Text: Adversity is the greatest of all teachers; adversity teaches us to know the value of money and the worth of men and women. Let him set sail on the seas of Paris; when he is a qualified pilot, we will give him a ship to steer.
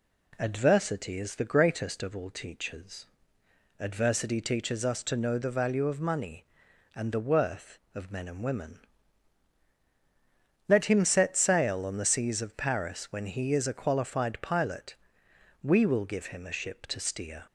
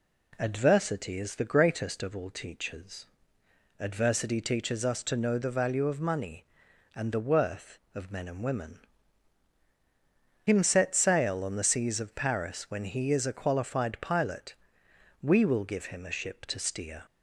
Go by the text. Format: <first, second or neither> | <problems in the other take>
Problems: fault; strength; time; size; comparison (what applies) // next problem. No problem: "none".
first | skips "Let"; at 9.6 s